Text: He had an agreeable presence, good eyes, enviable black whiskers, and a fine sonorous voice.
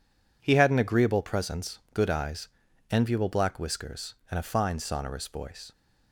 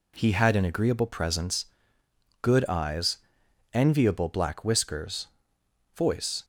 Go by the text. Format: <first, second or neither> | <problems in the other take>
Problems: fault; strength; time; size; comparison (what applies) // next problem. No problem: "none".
first | skips "and a fine sonorous"; at 5.6 s